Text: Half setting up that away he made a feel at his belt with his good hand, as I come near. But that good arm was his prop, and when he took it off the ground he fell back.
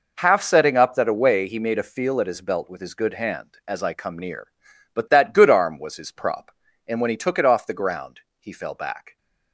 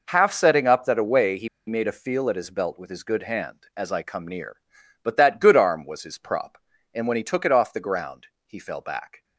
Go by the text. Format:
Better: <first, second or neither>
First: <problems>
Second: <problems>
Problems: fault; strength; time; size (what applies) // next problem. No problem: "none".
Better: first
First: pauses between "ground" and "he"; slight; at 8.2 s; 0.18 s long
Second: pauses between "he" and "made"; slight; at 1.4 s; 0.19 s long // pauses between "ground" and "he"; slight; at 8.2 s; 0.18 s long